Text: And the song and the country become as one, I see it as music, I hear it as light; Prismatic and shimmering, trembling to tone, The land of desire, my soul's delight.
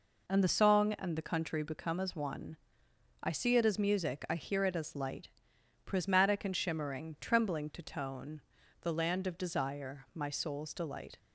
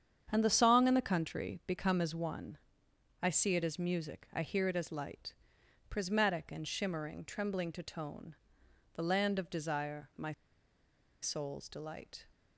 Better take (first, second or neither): first